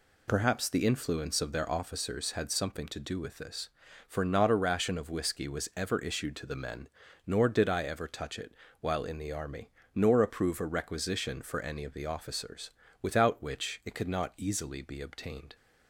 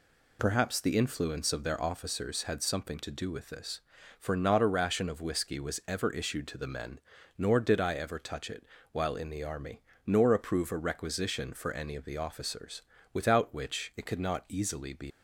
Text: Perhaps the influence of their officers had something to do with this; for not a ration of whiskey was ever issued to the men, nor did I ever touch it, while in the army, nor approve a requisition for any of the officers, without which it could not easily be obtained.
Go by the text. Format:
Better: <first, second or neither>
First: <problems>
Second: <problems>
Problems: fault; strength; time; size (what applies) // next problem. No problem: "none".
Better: first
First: none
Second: stops before "obtained"; at 15.1 s